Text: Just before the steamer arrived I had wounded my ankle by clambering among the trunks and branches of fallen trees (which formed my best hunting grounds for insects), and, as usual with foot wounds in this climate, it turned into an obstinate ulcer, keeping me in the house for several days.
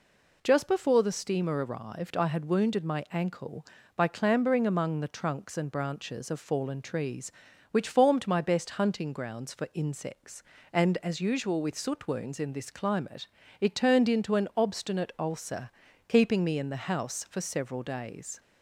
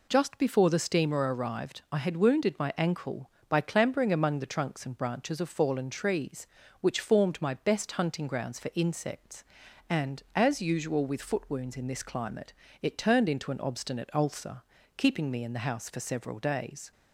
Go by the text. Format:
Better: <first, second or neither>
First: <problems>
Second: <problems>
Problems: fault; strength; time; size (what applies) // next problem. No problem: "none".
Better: second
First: says "soot" for "foot"; at 11.7 s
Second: none